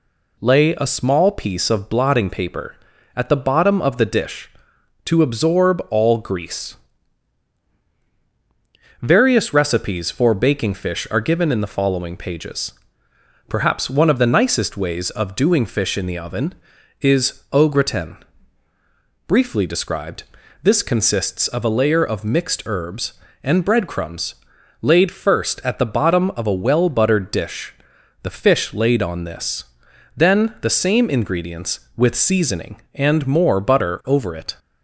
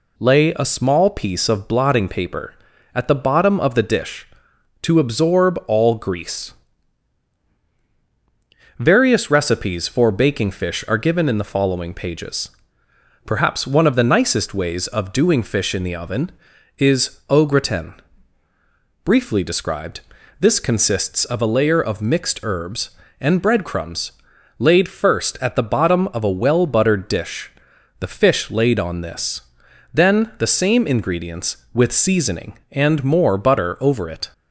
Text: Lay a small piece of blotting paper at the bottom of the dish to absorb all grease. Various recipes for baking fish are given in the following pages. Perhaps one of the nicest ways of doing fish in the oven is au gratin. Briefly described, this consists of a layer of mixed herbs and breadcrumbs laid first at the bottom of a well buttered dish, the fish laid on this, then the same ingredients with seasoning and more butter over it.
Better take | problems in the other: neither | pauses between "breadcrumbs" and "laid"; noticeable; the same in both

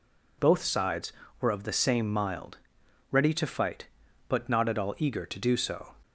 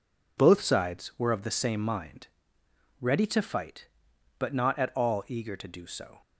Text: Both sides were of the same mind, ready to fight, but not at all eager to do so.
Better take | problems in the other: second | says "mild" for "mind"; at 2.1 s

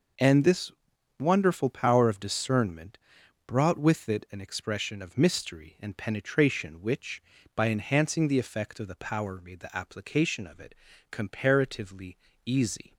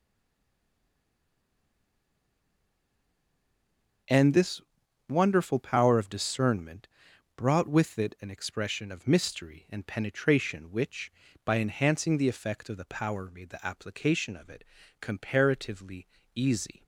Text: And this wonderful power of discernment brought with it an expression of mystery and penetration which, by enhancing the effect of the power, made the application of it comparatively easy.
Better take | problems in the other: first | stays silent before the first word; strong; until 4.0 s; 4.0 s long // pauses between "this" and "wonderful"; noticeable; at 4.6 s; 0.48 s long; noticeable in the first // pauses between "discernment" and "brought"; noticeable; at 6.8 s; 0.48 s long; noticeable in the first // pauses between "it" and "comparatively"; slight; at 14.6 s; 0.36 s long; slight in the first // pauses between "comparatively" and "easy"; slight; at 16.0 s; 0.28 s long; slight in the first

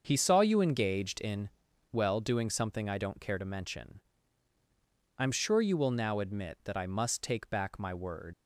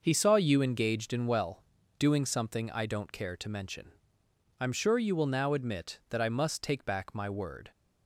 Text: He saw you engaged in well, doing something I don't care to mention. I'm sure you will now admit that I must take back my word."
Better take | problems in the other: second | starts louder than the rest; until 1.0 s; 6.5 dB // pauses between "in" and "well"; at 1.4 s; 0.42 s long // leaves "word" unfinished; at 8.3 s; 85 ms

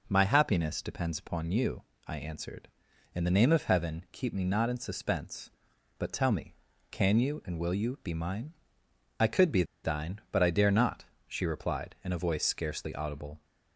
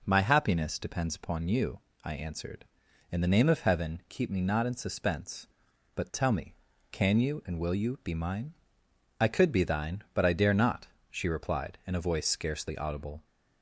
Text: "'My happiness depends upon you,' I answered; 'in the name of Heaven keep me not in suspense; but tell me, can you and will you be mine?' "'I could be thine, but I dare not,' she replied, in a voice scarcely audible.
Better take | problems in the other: second | pauses between "be" and "thine"; slight; at 9.6 s; 0.20 s long

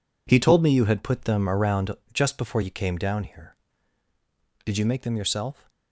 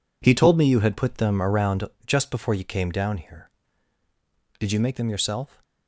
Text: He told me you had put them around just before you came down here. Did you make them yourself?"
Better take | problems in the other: neither | pauses between "around" and "just"; slight; the same in both

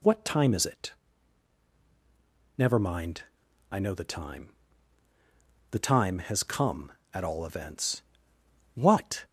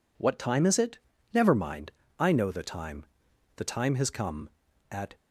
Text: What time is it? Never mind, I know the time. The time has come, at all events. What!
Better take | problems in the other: first | stops before "all events What"; at 5.1 s

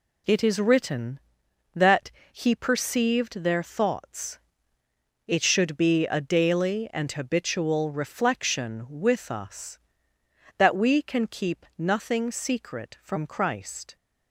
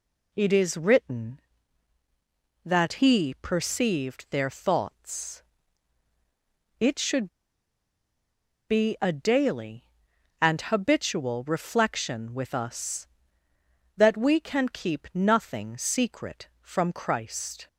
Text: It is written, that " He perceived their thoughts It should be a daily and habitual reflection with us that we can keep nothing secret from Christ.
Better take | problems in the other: first | pauses between "thoughts" and "It"; strong; at 5.4 s; 1.3 s long; noticeable in the first // pauses between "should" and "be"; strong; at 7.2 s; 1.4 s long

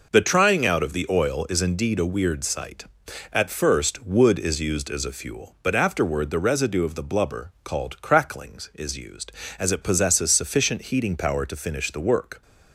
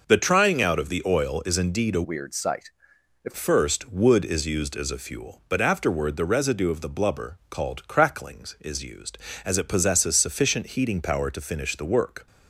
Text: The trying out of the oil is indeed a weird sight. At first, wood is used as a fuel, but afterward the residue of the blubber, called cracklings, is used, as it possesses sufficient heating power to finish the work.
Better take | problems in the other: first | changes voice from "weird" to "At"; from 2.0 to 3.3 s; 1.3 s long

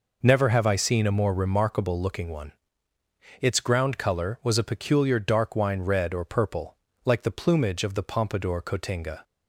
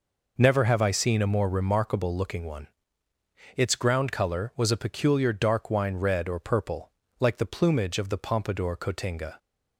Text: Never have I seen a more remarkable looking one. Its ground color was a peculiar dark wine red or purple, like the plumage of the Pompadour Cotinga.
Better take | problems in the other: neither | none

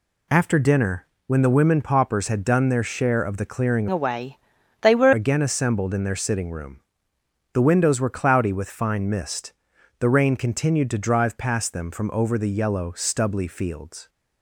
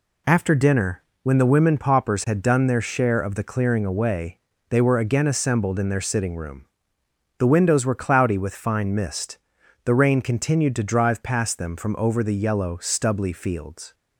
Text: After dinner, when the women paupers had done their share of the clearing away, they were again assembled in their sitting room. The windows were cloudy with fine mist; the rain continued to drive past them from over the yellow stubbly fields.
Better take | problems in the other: second | changes voice from "away" to "were"; from 3.9 to 5.1 s; 1.2 s long

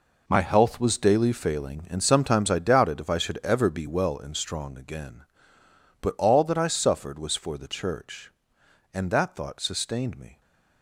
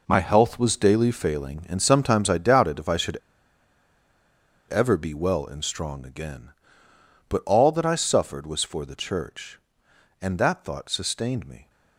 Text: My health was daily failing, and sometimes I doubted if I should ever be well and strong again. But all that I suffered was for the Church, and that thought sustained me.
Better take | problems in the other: first | pauses between "should" and "ever"; strong; at 3.1 s; 1.5 s long

